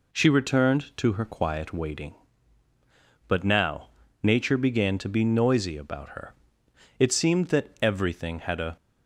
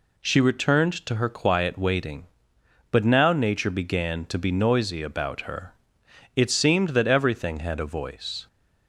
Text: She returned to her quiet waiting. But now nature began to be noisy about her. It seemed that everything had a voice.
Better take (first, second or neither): second